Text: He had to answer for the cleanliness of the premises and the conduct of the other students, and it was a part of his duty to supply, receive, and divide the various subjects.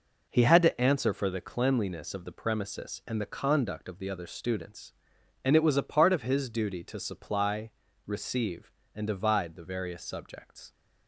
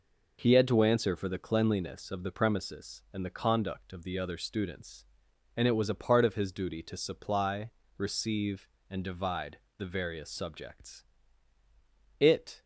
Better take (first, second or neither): first